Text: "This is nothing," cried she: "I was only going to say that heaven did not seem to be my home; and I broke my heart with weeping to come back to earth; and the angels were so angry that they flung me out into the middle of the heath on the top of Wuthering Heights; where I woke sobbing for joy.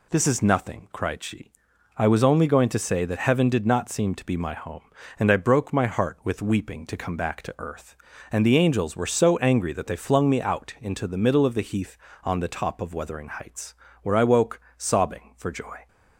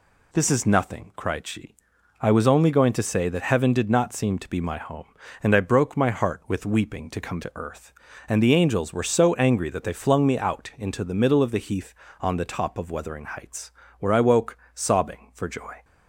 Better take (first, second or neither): first